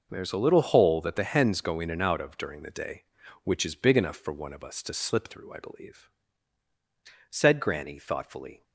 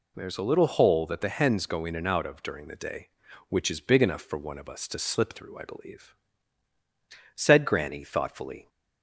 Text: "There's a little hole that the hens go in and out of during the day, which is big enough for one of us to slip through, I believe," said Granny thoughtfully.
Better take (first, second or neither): second